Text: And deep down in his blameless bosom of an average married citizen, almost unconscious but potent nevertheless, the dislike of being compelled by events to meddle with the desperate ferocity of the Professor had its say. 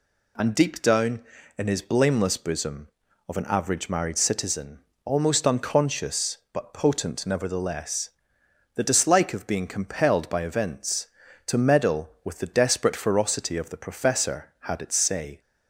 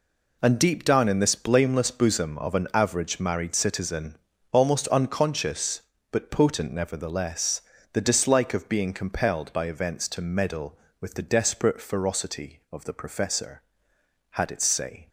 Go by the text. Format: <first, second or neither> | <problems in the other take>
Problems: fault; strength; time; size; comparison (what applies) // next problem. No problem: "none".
first | says "this" for "his"; at 1.1 s